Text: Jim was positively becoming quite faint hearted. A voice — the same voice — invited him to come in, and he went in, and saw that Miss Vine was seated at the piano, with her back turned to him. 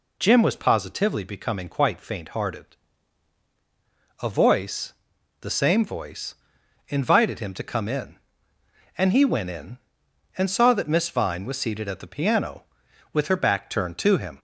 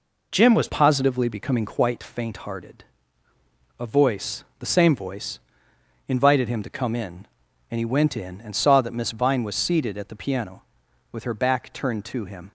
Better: first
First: none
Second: changes voice at "positively"; from 0.6 s on; 11.9 s long

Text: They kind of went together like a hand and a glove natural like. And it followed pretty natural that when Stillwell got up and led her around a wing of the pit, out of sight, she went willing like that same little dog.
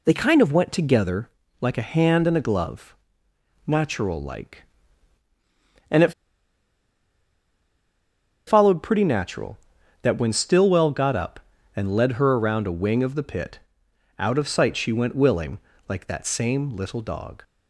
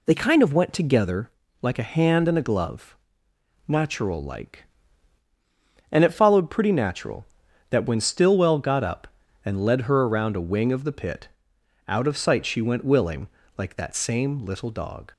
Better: second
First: pauses between "together" and "like"; slight; at 1.2 s; 0.32 s long // pauses between "glove" and "natural"; noticeable; at 2.9 s; 0.72 s long // pauses between "it" and "followed"; strong; at 6.1 s; 2.3 s long // pauses between "willing" and "like"; slight; at 15.5 s; 0.30 s long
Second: pauses between "together" and "like"; slight; at 1.2 s; 0.32 s long // pauses between "glove" and "natural"; noticeable; at 2.9 s; 0.72 s long // pauses between "willing" and "like"; slight; at 13.2 s; 0.30 s long

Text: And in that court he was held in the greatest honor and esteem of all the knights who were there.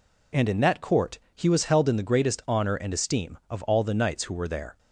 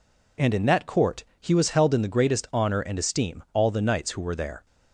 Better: first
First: pauses between "court" and "he"; slight; at 1.1 s; 0.16 s long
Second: pauses between "court" and "he"; slight; at 1.2 s; 0.16 s long // skips "of"; at 3.4 s

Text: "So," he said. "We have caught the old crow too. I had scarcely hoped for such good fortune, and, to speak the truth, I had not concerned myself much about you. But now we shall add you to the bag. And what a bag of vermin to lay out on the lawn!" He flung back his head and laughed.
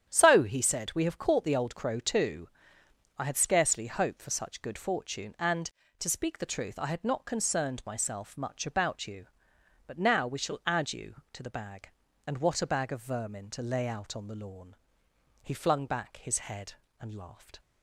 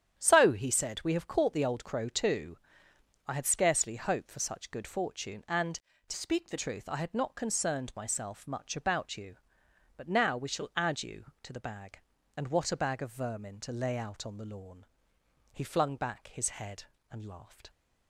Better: first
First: starts louder than the rest; strong; until 1.1 s; 9.5 dB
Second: starts louder than the rest; strong; until 1.2 s; 9.5 dB // changes voice from "speak" to "the"; from 6.1 to 6.5 s; 0.4 s long

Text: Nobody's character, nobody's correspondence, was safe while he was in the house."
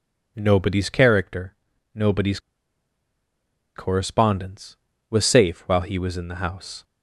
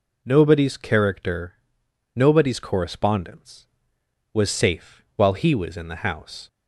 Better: second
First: pauses between "nobody's" and "correspondence"; strong; at 2.4 s; 1.3 s long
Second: none

